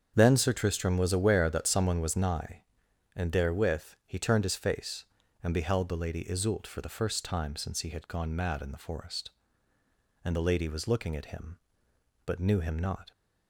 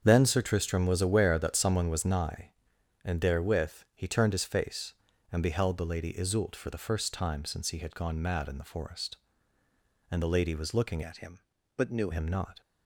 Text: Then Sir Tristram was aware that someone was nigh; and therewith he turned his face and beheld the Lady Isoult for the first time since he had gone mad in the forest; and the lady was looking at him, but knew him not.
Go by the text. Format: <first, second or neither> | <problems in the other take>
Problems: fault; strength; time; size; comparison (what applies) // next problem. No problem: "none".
first | starts louder than the rest; strong; until 1.0 s; 7.5 dB; strong in the first // changes voice from "at" to "knew"; from 11.0 to 12.0 s; 1.0 s long